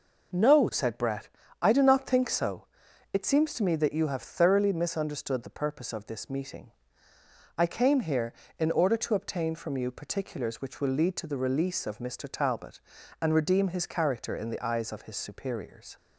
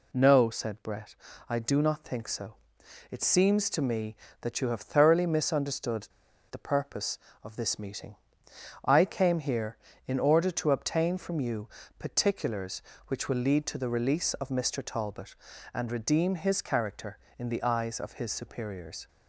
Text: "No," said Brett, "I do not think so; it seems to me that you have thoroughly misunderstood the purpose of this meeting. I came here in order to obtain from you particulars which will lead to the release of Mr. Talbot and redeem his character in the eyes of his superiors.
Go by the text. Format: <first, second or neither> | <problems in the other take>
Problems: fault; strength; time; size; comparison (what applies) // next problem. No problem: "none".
first | pauses between "misunderstood" and "the"; at 6.0 s; 0.44 s long // pauses between "you" and "particulars"; slight; at 11.6 s; 0.30 s long